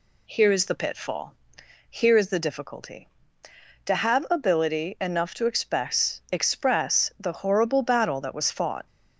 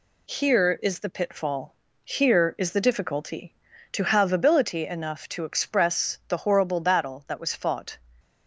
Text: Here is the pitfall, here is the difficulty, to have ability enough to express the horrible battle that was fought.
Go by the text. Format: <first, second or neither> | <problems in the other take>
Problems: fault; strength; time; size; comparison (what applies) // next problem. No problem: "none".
second | says "express" twice; at 6.3 s